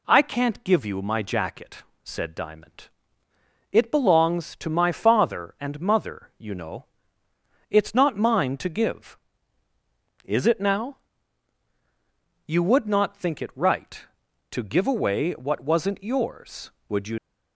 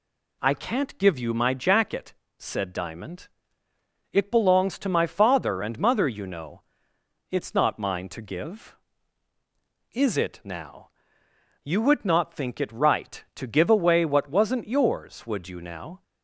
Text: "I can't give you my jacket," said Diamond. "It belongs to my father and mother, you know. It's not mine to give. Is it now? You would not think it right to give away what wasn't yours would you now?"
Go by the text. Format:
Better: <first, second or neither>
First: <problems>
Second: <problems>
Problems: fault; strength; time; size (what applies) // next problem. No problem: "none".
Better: second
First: stops before "now"; at 17.1 s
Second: none